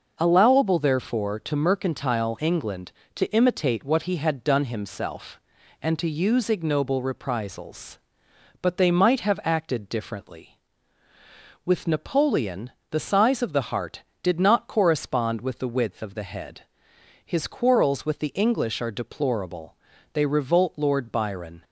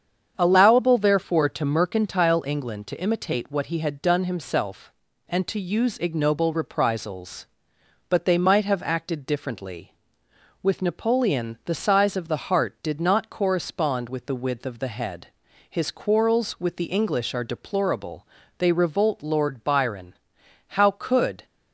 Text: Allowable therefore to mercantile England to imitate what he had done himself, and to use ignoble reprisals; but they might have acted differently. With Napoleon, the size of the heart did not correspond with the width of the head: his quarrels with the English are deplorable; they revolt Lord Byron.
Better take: first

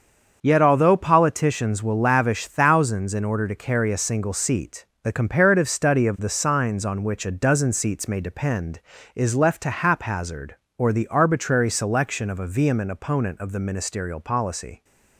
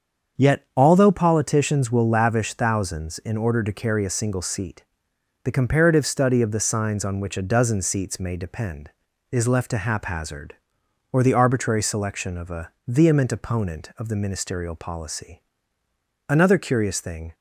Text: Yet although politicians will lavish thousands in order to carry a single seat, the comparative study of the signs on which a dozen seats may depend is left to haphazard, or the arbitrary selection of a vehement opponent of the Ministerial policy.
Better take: first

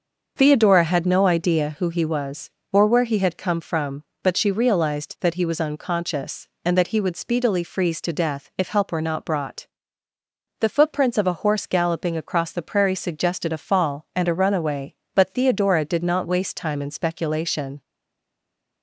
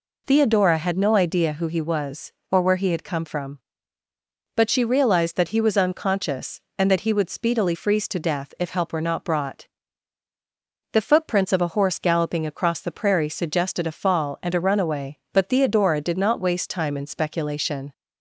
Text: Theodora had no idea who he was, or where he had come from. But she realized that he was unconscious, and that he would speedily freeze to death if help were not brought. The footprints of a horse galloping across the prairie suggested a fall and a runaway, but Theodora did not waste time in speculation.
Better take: second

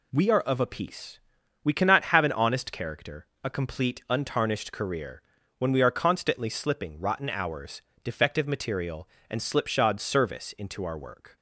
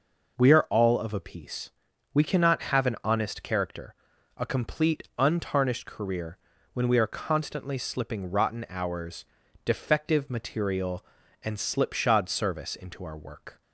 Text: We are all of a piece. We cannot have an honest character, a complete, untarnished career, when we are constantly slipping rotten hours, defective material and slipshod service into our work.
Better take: second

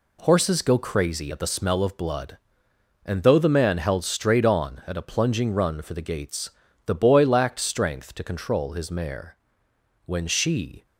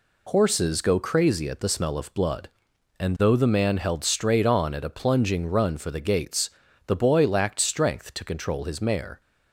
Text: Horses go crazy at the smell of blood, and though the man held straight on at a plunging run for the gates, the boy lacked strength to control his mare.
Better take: second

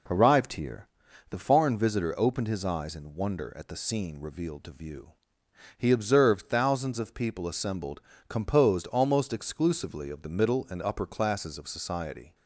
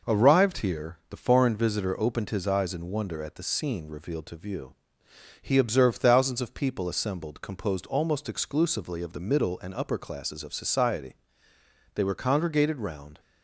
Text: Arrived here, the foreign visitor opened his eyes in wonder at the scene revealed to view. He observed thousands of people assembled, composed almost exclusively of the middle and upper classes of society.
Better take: first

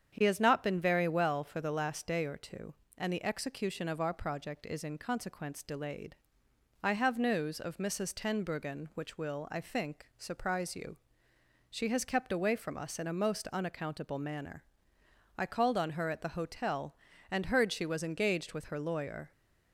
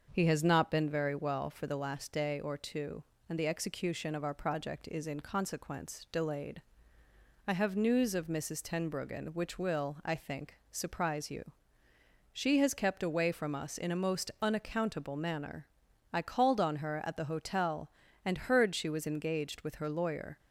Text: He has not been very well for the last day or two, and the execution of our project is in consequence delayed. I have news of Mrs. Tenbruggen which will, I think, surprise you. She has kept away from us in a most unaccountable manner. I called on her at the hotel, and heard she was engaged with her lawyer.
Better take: neither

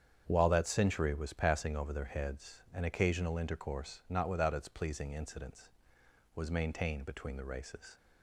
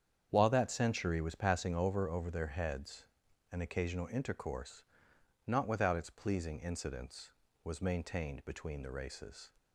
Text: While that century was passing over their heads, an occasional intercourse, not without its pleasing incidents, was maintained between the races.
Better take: first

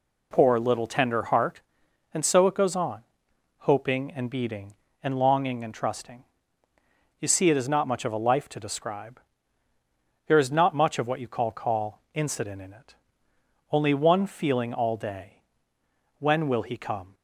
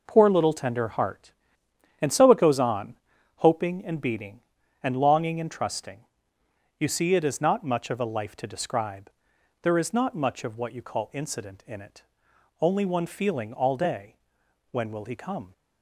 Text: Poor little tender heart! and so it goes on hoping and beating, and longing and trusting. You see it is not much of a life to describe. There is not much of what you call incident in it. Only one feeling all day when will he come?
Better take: second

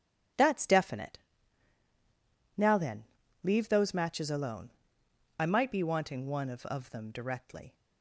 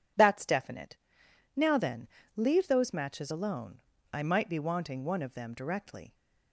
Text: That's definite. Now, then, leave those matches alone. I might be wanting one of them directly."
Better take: second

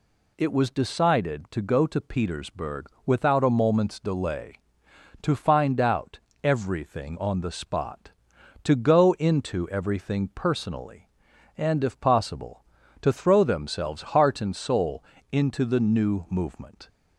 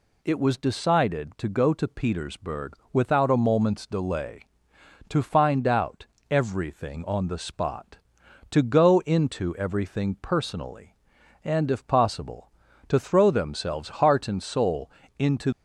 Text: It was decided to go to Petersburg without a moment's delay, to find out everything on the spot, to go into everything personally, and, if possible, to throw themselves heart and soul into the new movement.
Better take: first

